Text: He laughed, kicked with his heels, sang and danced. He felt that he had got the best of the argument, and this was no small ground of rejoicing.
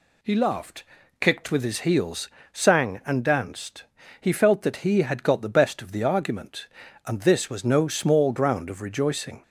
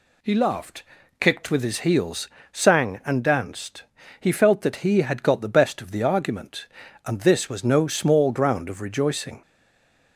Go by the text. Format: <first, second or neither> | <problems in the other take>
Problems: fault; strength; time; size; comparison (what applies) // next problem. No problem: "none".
first | stays silent after the last word; slight; from 9.4 s on; 0.7 s long